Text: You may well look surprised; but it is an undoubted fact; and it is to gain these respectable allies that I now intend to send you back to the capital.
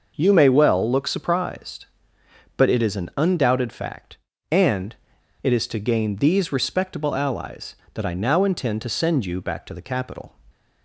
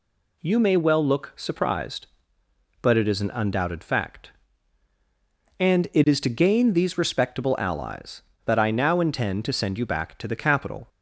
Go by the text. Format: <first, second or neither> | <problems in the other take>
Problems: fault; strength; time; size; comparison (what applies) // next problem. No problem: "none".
second | starts louder than the rest; noticeable; until 1.1 s; 6 dB // pauses between "and" and "it"; noticeable; at 4.9 s; 0.48 s long